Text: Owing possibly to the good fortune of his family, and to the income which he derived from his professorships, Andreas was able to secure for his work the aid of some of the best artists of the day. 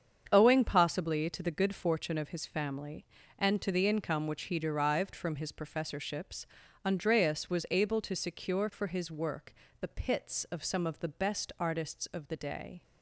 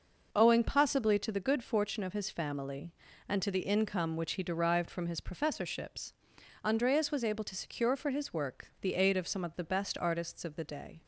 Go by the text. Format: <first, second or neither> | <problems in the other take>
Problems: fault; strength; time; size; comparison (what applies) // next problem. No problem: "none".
second | starts louder than the rest; strong; until 1.3 s; 7.5 dB // pauses between "work" and "the"; slight; at 9.5 s; 0.28 s long // says "pits" for "aid"; at 9.8 s